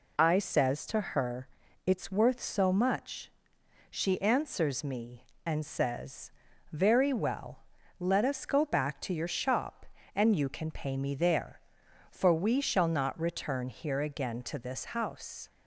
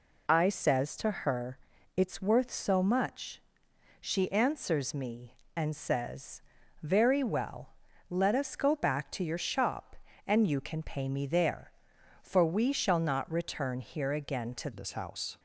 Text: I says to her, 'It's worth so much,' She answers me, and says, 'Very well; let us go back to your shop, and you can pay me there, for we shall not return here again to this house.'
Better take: first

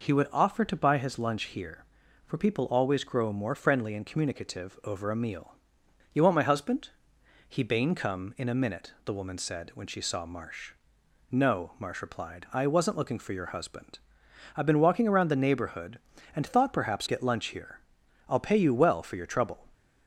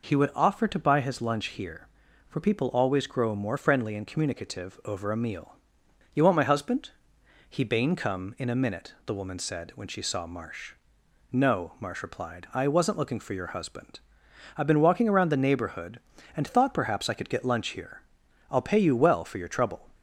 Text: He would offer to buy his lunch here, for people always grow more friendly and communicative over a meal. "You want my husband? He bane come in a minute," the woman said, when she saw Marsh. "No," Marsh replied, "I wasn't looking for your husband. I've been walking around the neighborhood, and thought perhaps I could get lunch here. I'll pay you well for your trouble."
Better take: second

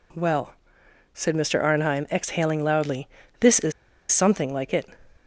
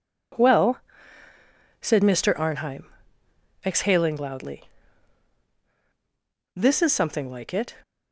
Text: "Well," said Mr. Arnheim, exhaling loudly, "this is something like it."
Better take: second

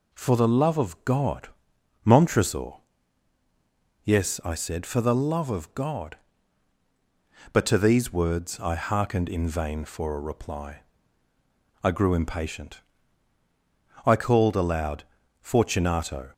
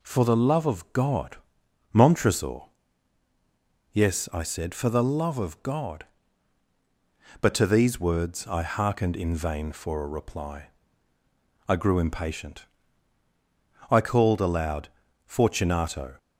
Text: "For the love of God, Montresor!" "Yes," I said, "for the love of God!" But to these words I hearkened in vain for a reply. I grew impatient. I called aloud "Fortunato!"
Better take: neither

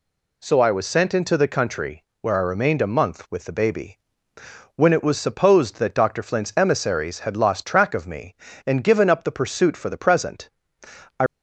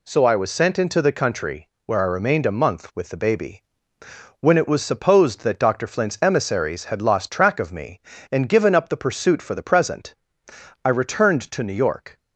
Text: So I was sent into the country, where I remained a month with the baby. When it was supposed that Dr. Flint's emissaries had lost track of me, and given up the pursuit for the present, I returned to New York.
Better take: second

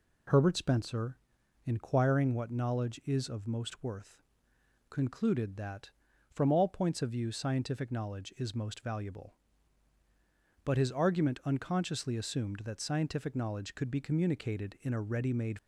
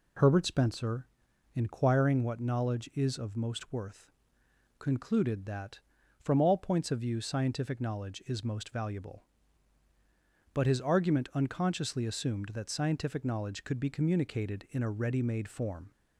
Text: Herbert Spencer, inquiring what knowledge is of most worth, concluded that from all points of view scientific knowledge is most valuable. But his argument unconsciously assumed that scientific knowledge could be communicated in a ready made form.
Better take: second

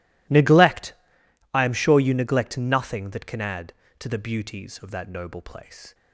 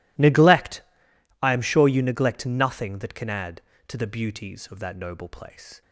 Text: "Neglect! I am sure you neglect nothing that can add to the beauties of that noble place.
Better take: neither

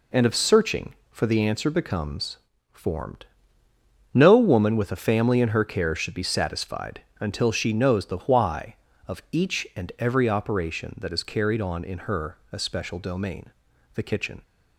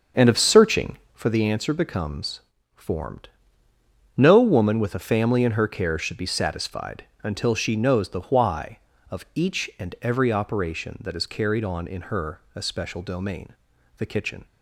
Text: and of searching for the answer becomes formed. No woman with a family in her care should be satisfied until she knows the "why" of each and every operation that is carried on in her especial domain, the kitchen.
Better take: first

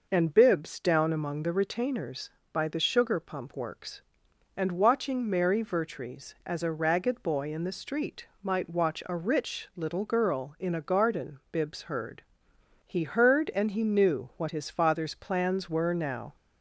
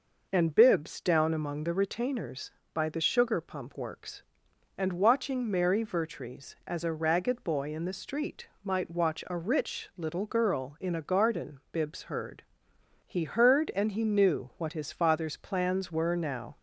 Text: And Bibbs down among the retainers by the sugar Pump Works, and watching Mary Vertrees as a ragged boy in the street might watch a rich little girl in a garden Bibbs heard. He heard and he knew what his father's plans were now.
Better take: neither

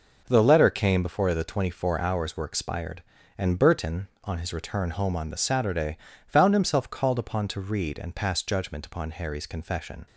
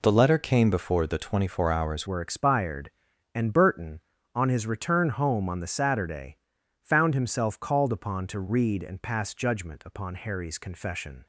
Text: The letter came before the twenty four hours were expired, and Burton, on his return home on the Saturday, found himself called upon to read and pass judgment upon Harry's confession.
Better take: first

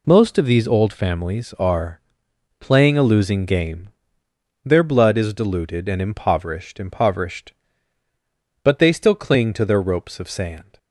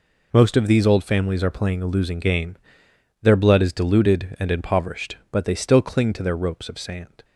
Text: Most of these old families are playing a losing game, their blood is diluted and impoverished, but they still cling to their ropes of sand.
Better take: second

